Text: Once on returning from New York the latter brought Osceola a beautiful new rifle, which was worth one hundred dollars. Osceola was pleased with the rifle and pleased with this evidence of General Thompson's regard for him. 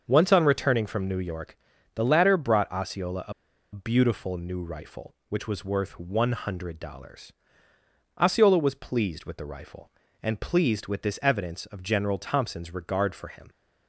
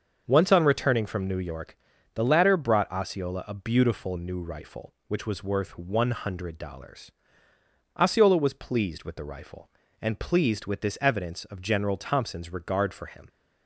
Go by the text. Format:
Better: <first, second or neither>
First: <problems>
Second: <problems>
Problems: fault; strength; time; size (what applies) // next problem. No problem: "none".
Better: second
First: starts louder than the rest; until 1.0 s; 6.5 dB // pauses between "York" and "the"; at 1.5 s; 0.38 s long // pauses between "a" and "beautiful"; at 3.3 s; 0.40 s long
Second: starts louder than the rest; until 1.2 s; 6.5 dB // pauses between "York" and "the"; at 1.7 s; 0.38 s long